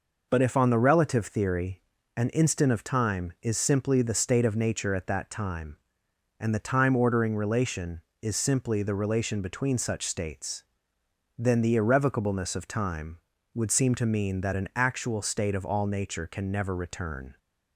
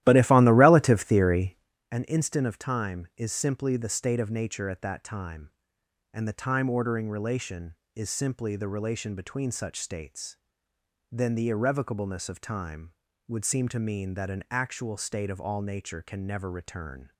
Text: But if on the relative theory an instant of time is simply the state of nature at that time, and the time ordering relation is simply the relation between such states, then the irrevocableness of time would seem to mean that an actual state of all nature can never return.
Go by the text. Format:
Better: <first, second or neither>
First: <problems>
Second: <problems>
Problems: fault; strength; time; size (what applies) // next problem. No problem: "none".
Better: first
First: pauses between "theory" and "an"; slight; at 1.8 s; 0.34 s long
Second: starts louder than the rest; strong; until 1.7 s; 14 dB // pauses between "theory" and "an"; slight; at 1.5 s; 0.34 s long